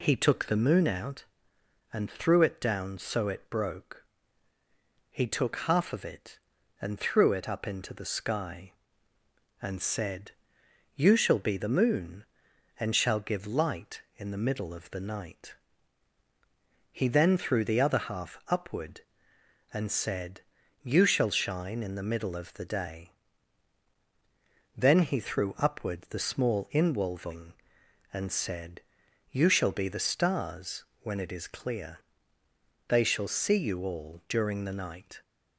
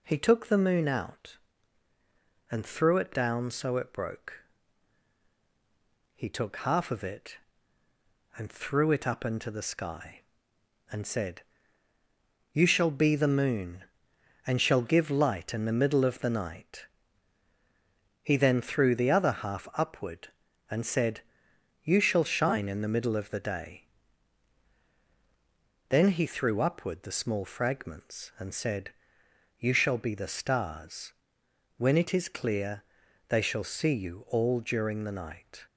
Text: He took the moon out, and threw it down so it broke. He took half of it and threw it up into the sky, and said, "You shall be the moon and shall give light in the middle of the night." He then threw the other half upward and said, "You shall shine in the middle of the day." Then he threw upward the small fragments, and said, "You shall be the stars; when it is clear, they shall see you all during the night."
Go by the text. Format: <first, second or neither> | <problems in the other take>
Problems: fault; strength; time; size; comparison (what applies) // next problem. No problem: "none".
second | says "inwolving" for "fragments"; at 26.7 s